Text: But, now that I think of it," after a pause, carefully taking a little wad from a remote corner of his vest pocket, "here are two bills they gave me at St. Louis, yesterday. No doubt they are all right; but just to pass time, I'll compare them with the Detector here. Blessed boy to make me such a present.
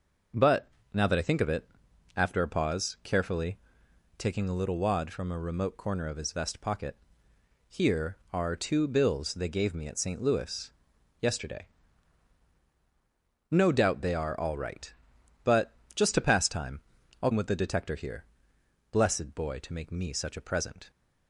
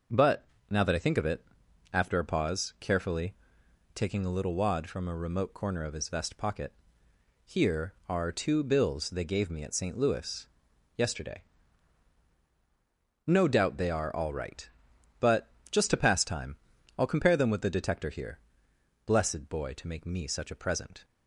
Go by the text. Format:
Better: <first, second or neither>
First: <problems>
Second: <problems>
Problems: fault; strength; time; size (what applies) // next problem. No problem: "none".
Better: second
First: pauses between "carefully" and "taking"; noticeable; at 3.5 s; 0.60 s long // pauses between "but" and "just"; slight; at 15.7 s; 0.22 s long // skips "compare them"; at 17.3 s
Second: pauses between "carefully" and "taking"; noticeable; at 3.3 s; 0.60 s long // pauses between "but" and "just"; slight; at 15.4 s; 0.22 s long